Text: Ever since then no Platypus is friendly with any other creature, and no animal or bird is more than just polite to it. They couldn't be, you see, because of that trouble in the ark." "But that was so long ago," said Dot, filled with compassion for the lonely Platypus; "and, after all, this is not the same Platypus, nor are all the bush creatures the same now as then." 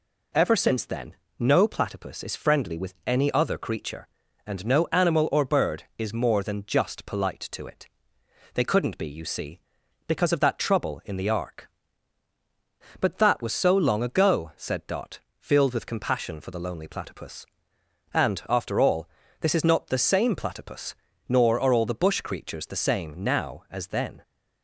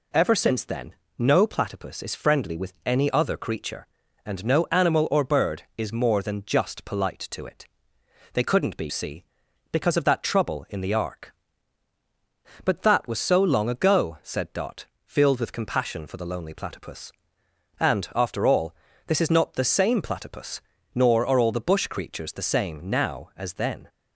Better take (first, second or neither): first